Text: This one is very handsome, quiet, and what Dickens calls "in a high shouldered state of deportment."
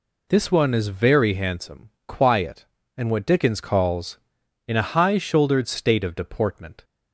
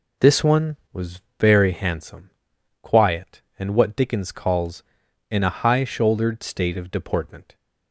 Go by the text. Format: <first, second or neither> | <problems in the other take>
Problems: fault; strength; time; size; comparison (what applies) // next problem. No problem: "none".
first | says "was" for "is"; at 0.9 s